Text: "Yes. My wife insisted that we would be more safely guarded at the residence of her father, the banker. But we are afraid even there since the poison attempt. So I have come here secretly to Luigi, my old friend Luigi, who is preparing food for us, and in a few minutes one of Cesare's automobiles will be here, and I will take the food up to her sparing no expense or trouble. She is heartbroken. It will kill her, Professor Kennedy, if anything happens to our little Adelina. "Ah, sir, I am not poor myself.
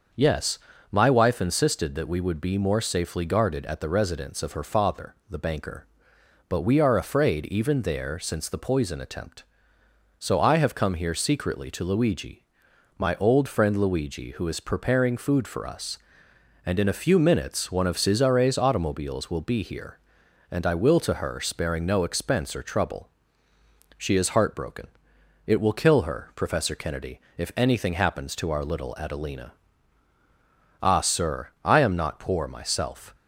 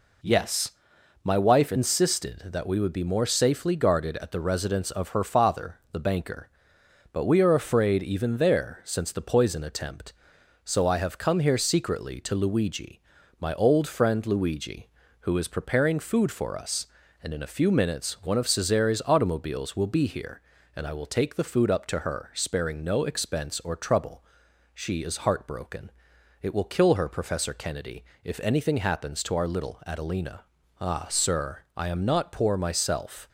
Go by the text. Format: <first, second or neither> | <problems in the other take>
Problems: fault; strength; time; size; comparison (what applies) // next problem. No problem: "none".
second | starts louder than the rest; until 1.5 s; 6.5 dB // skips "take the food up"; at 21.0 s